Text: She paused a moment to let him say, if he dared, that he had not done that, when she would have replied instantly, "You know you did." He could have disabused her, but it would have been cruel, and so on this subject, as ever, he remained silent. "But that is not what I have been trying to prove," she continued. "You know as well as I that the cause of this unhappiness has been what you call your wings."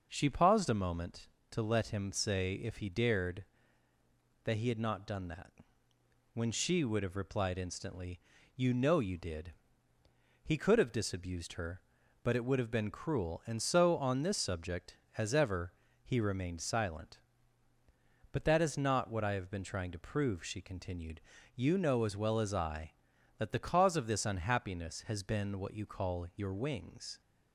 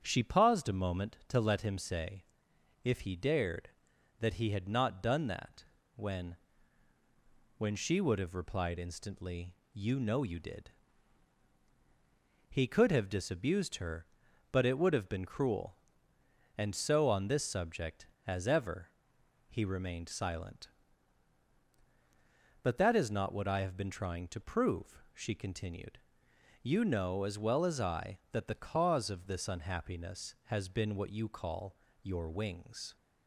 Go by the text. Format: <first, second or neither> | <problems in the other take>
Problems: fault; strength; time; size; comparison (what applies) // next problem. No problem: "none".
first | starts louder than the rest; strong; until 1.0 s; 8 dB; noticeable in the first // says "when" twice; at 7.5 s // pauses between "call" and "your"; slight; at 31.7 s; 0.26 s long